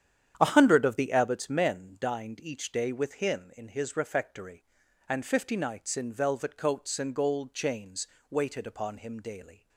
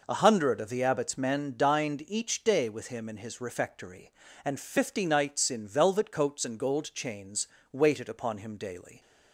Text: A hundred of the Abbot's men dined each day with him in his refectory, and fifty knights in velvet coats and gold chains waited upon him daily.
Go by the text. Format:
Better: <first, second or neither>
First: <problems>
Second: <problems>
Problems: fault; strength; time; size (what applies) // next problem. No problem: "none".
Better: second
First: starts louder than the rest; strong; until 1.4 s; 9.5 dB // pauses between "chains" and "waited"; slight; at 8.0 s; 0.22 s long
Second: pauses between "chains" and "waited"; slight; at 7.4 s; 0.26 s long